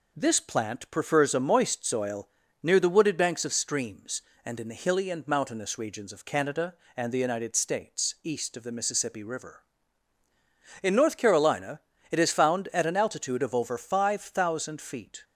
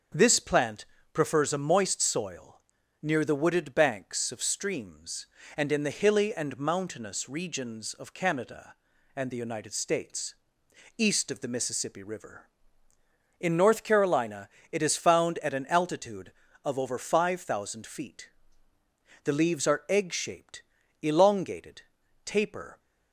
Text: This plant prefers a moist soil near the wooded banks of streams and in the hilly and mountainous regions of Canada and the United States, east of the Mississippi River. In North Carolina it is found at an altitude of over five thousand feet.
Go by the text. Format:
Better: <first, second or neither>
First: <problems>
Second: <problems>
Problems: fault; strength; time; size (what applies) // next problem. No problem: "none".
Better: first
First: pauses between "soil" and "near"; slight; at 2.2 s; 0.34 s long // pauses between "Carolina" and "it"; slight; at 11.7 s; 0.32 s long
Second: starts louder than the rest; strong; until 1.4 s; 7.5 dB // pauses between "plant" and "prefers"; slight; at 0.8 s; 0.30 s long // pauses between "soil" and "near"; at 2.5 s; 0.42 s long // pauses between "Carolina" and "it"; slight; at 14.4 s; 0.22 s long // goes on to say "The leaves are egg shaped elongated taper"; strong; from 19.2 s on; 3.5 s long